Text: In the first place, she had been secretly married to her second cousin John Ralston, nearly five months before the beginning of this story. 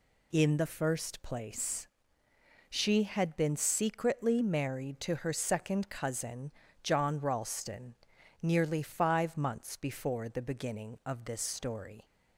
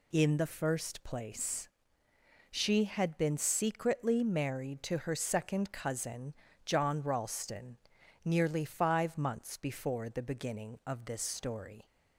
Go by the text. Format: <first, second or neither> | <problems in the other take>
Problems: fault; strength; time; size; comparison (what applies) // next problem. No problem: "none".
neither | pauses between "cousin" and "John"; slight; the same in both